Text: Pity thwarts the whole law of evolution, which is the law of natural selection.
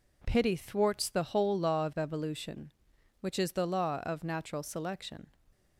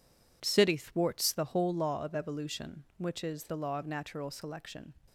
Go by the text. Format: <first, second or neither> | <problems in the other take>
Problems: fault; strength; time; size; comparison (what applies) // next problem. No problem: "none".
first | says "City" for "Pity"; at 0.4 s